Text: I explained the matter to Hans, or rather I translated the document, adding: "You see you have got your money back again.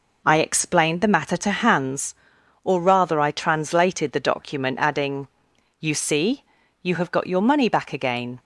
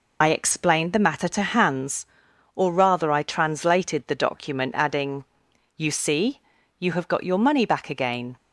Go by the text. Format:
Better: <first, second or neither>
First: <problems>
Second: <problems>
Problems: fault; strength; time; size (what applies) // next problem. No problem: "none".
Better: first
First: pauses between "see" and "you"; at 6.4 s; 0.38 s long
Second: loses the start of "I"; at 0.2 s; 45 ms // pauses between "see" and "you"; at 6.4 s; 0.38 s long